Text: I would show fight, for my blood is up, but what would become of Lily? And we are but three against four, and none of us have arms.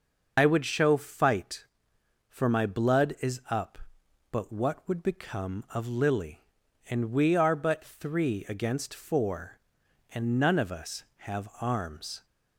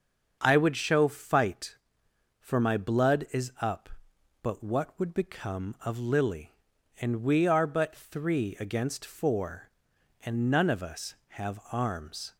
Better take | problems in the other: second | loses the start of "I"; at 0.3 s; 85 ms // starts louder than the rest; until 1.3 s; 6 dB; also in the second

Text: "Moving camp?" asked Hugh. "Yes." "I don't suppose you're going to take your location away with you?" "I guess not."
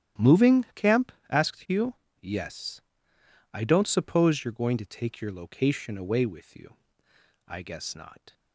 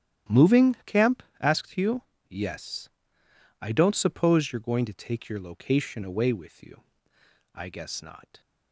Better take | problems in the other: neither | starts louder than the rest; strong; the same in both

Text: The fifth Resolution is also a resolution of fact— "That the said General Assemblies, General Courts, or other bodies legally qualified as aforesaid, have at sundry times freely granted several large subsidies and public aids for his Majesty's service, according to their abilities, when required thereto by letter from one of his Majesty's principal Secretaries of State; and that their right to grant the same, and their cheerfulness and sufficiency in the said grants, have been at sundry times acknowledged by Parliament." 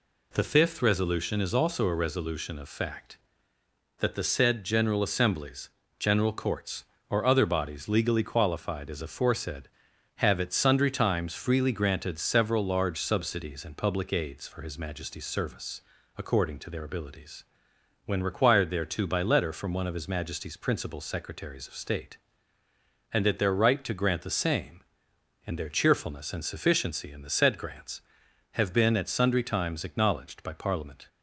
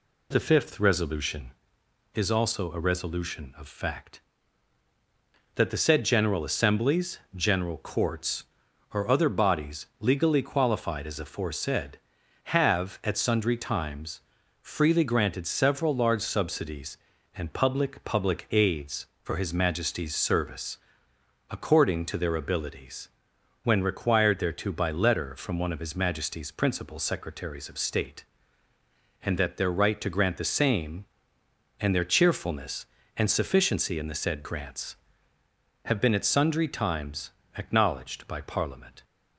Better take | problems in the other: first | pauses between "times" and "freely"; at 14.2 s; 0.40 s long // says "public" twice; at 18.0 s // pauses between "times" and "acknowledged"; slight; at 37.2 s; 0.26 s long

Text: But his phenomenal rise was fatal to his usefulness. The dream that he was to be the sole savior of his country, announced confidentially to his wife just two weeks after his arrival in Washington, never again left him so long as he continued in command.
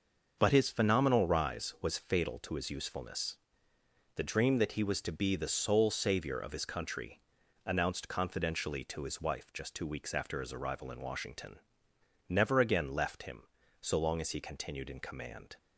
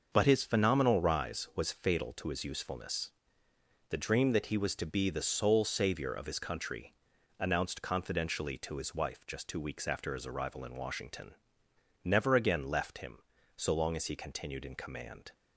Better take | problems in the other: neither | starts louder than the rest; the same in both

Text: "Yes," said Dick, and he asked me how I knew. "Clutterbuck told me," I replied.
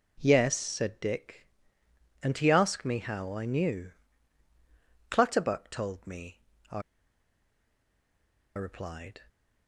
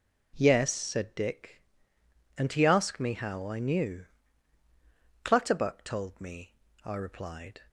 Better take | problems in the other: second | pauses between "I" and "replied"; strong; at 6.8 s; 1.7 s long

